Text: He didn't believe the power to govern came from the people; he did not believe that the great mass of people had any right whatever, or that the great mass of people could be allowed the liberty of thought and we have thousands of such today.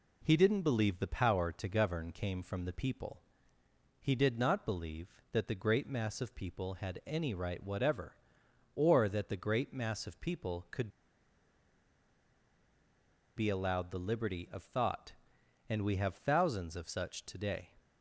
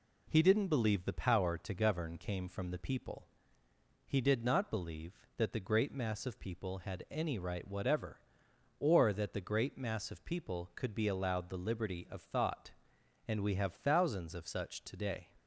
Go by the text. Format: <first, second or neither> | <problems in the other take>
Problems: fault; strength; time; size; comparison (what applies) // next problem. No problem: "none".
second | pauses between "could" and "be"; strong; at 10.8 s; 2.4 s long